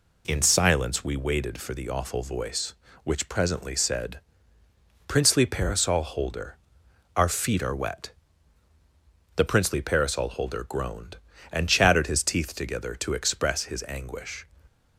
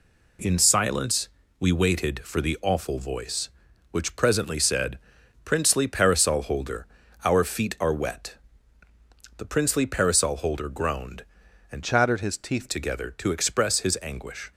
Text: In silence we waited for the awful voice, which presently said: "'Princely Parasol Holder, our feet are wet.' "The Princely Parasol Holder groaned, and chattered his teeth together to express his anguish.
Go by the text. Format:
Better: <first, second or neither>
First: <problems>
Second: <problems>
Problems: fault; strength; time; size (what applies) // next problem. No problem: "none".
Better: first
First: none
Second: pauses between "silence" and "we"; slight; at 1.2 s; 0.32 s long // changes voice from "chattered" to "teeth"; from 11.8 to 12.6 s; 0.8 s long